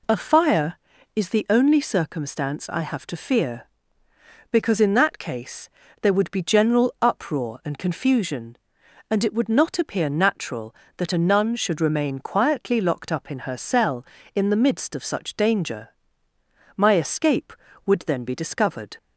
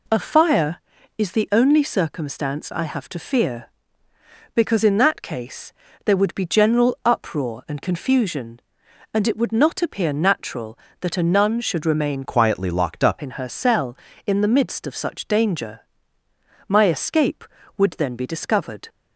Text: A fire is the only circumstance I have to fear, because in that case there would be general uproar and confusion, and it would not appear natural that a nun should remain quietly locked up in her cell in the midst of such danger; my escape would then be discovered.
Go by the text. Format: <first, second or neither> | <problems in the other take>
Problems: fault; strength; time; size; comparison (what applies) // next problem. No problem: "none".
first | pauses between "case" and "there"; slight; at 5.7 s; 0.32 s long; slight in the first // changes voice from "quietly" to "up"; from 12.2 to 13.1 s; 0.9 s long